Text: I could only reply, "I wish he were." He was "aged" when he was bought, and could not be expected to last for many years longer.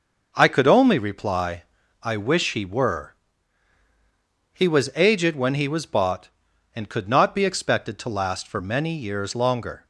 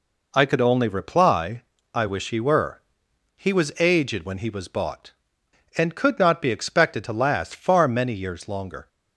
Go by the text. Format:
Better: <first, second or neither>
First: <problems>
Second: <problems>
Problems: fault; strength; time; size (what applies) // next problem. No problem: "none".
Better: first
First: none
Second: says "far" for "for"; at 7.5 s